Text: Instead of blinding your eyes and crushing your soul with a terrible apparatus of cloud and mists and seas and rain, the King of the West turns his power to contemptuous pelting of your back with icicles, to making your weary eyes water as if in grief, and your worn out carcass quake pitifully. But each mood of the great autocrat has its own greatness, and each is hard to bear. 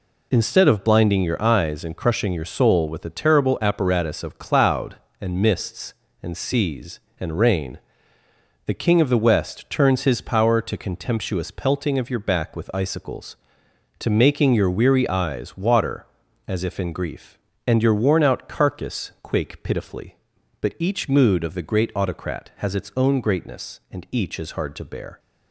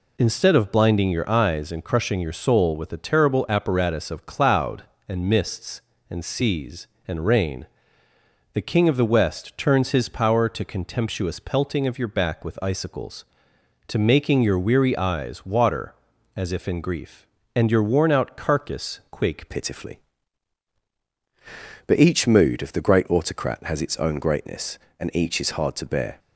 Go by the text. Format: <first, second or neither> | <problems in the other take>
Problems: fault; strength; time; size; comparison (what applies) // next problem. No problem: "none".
first | changes voice at "pitifully"; from 19.4 s on; 6.7 s long